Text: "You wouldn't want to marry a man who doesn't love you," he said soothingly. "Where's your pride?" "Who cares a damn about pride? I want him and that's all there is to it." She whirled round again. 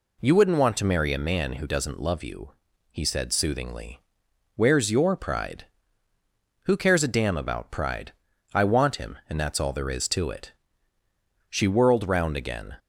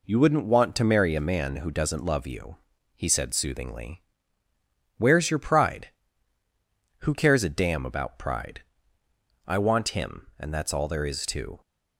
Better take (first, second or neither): first